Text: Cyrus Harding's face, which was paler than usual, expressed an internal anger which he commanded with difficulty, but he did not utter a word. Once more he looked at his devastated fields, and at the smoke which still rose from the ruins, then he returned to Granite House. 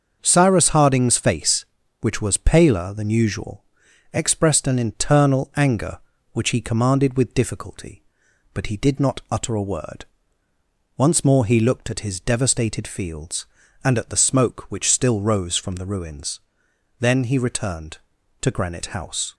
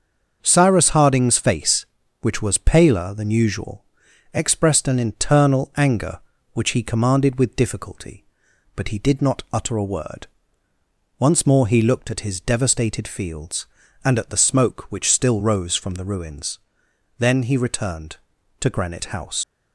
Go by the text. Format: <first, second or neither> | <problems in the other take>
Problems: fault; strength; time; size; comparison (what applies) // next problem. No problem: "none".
first | starts louder than the rest; until 1.4 s; 6.5 dB; also in the first // leaves "House" unfinished; at 19.4 s; 95 ms